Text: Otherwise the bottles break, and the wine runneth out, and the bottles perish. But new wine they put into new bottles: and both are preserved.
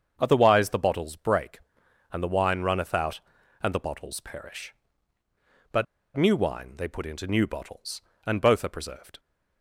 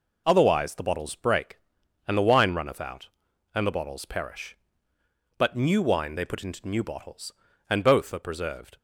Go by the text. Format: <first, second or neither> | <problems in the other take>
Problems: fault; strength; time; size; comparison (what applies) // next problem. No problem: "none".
second | starts louder than the rest; strong; until 1.2 s; 7 dB // pauses between "But" and "new"; slight; at 5.8 s; 0.31 s long